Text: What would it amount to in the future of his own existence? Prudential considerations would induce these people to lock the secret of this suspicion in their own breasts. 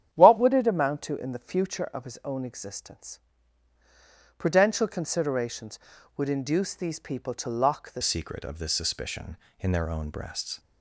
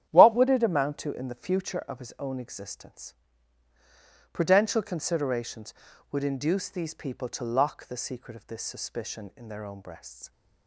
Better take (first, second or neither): second